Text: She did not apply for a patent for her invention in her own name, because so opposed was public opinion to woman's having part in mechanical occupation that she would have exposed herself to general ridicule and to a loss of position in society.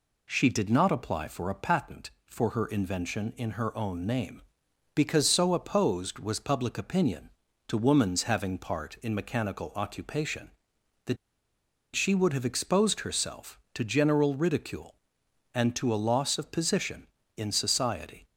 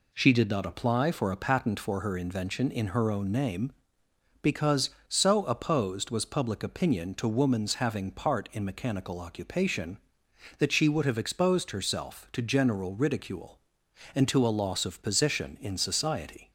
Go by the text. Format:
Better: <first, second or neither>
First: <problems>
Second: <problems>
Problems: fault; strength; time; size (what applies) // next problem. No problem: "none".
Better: second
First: pauses between "that" and "she"; noticeable; at 11.1 s; 0.78 s long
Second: none